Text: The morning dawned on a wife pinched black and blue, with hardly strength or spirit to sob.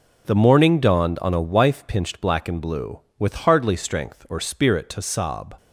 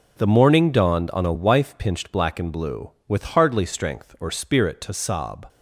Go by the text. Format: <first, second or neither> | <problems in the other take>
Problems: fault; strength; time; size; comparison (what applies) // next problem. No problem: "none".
neither | none